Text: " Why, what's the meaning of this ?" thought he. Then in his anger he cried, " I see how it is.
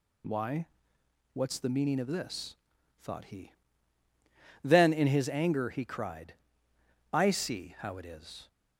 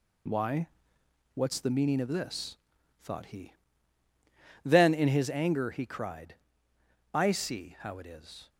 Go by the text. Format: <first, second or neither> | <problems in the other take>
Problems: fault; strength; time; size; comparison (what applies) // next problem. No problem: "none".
first | gets quieter; strong; throughout; 9.5 dB